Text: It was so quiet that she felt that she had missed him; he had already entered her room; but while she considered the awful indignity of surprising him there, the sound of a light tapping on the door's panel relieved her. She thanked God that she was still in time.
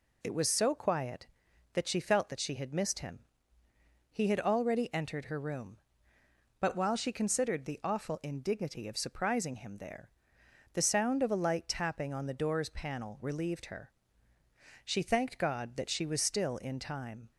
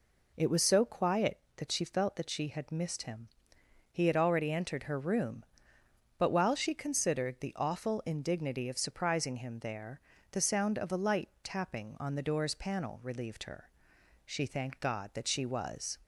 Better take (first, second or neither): first